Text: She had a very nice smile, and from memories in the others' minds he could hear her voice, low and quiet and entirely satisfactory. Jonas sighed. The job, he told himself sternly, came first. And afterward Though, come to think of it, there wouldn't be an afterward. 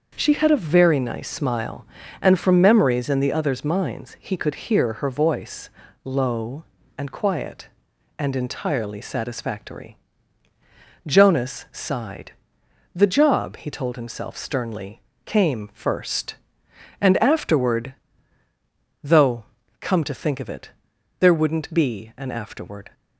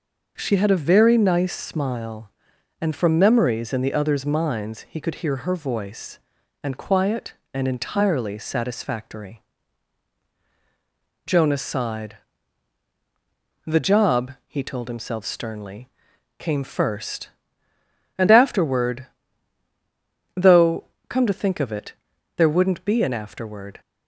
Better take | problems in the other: first | starts louder than the rest; until 1.3 s; 6 dB; also in the first // skips "low"; at 6.4 s // pauses between "afterward" and "Though"; strong; at 19.0 s; 1.3 s long; also in the first

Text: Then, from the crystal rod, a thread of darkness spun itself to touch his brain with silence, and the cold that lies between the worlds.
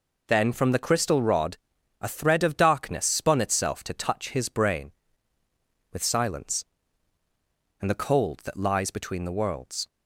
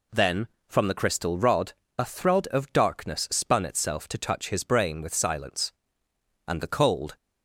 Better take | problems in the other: first | stops before "that lies between the worlds"; at 7.1 s

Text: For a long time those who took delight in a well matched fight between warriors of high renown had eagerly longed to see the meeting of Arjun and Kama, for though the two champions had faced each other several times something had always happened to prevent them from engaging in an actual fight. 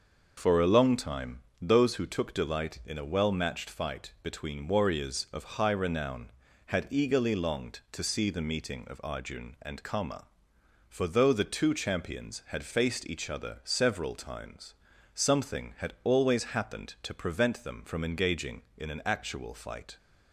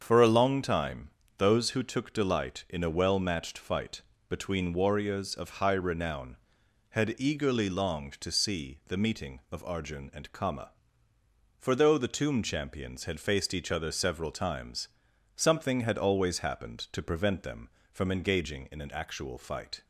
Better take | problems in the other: first | starts louder than the rest; until 1.0 s; 7 dB // pauses between "time" and "those"; slight; at 1.1 s; 0.26 s long; slight in the first // pauses between "fight" and "between"; slight; at 4.0 s; 0.26 s long // says "tomb" for "two"; at 12.1 s // pauses between "times" and "something"; noticeable; at 14.8 s; 0.48 s long; also in the first

